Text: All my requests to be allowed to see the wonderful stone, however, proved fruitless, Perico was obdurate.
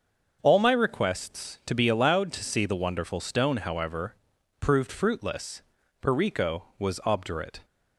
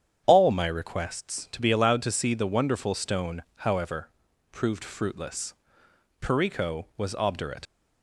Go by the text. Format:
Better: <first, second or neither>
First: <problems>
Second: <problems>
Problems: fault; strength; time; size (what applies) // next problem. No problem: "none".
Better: first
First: starts louder than the rest; until 1.4 s; 6.5 dB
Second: starts louder than the rest; strong; until 1.2 s; 8.5 dB // leaves "obdurate" unfinished; at 7.6 s; 55 ms